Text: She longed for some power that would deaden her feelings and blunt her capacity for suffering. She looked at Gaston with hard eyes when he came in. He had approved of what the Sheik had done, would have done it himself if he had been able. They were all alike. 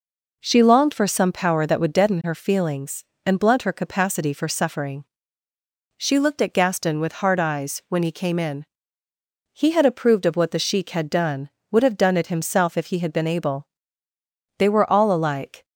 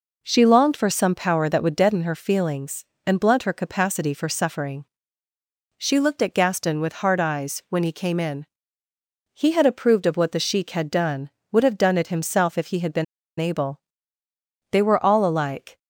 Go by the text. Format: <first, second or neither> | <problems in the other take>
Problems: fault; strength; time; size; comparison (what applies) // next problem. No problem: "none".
first | pauses between "been" and "able"; slight; at 13.0 s; 0.35 s long